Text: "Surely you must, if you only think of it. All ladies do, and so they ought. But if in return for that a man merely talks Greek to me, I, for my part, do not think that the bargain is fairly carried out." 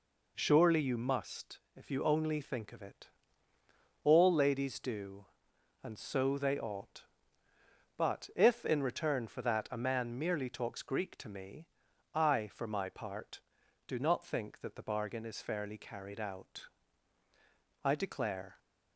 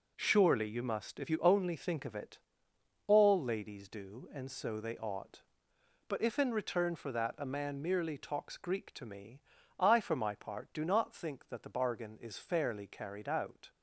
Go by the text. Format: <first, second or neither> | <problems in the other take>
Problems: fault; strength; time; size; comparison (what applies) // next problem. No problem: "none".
second | goes on to say "I declare"; noticeable; from 17.8 s on; 0.74 s long